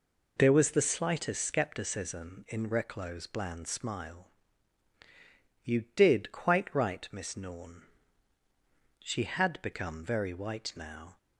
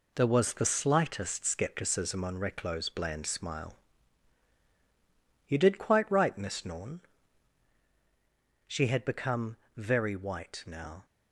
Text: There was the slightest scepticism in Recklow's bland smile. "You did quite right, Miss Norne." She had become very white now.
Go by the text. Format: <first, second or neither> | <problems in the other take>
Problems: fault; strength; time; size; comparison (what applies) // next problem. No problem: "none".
first | says "on" for "in"; at 2.2 s // pauses between "become" and "very"; slight; at 9.5 s; 0.18 s long